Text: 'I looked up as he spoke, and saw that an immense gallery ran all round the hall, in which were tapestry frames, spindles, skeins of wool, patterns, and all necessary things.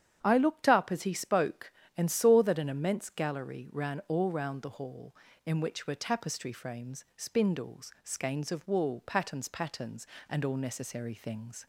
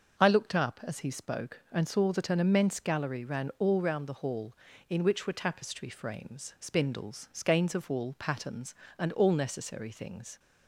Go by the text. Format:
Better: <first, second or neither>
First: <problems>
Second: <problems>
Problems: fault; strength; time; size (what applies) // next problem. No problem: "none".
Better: second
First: starts louder than the rest; strong; until 1.2 s; 9 dB // says "patterns" twice; at 9.4 s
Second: starts louder than the rest; until 1.2 s; 6.5 dB